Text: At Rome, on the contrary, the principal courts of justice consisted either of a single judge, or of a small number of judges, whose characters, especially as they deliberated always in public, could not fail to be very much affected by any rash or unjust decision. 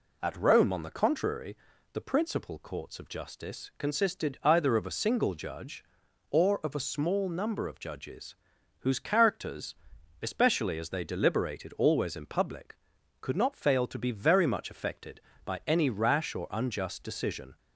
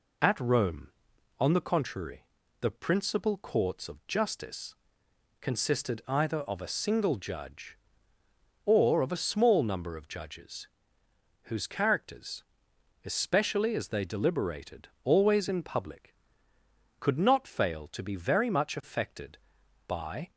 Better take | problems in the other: first | pauses between "justice" and "consisted"; noticeable; at 4.7 s; 0.68 s long // pauses between "deliberated" and "always"; slight; at 14.8 s; 0.16 s long // stops before "any rash or unjust decision"; at 20.3 s

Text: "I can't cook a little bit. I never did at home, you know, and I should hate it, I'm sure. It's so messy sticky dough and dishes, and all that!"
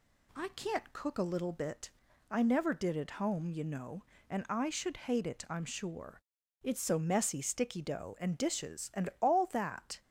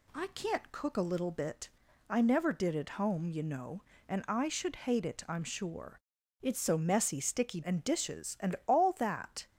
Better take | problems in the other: first | skips "dough"; at 7.6 s

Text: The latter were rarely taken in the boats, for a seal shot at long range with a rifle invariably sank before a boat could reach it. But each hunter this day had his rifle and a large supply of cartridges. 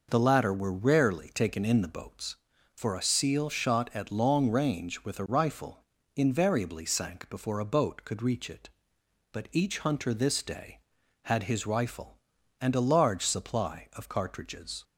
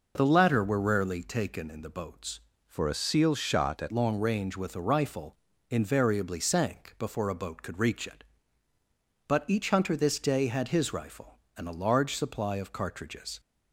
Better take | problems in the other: first | changes voice from "for" to "at"; from 2.6 to 3.9 s; 1.3 s long // pauses between "rifle" and "invariably"; slight; at 5.3 s; 0.32 s long; slight in the first

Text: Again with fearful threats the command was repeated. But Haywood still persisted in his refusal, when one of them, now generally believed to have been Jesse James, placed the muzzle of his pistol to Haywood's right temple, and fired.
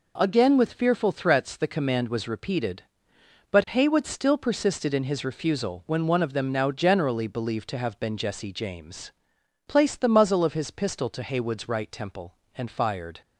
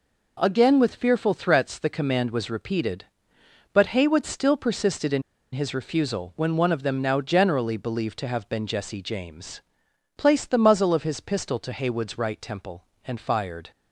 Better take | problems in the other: first | pauses between "in" and "his"; slight; at 5.2 s; 0.32 s long

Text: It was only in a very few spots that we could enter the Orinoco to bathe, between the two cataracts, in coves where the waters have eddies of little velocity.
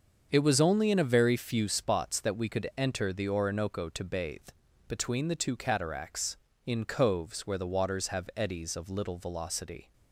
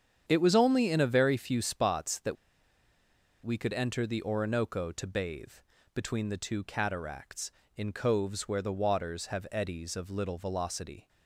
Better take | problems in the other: first | starts louder than the rest; strong; until 1.2 s; 8 dB; also in the first // pauses between "that" and "we"; at 2.3 s; 1.0 s long

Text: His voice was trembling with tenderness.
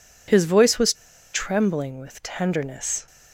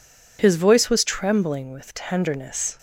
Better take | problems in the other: second | pauses between "was" and "trembling"; at 0.9 s; 0.40 s long

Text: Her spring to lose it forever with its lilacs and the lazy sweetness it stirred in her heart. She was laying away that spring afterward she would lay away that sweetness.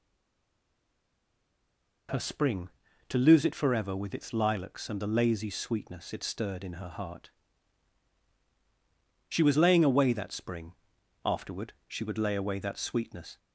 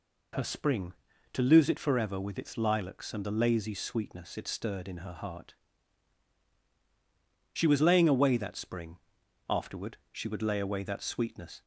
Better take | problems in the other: second | stays silent before the first word; noticeable; until 2.0 s; 2.0 s long // pauses between "spring" and "afterward"; noticeable; at 10.7 s; 0.50 s long; noticeable in the second

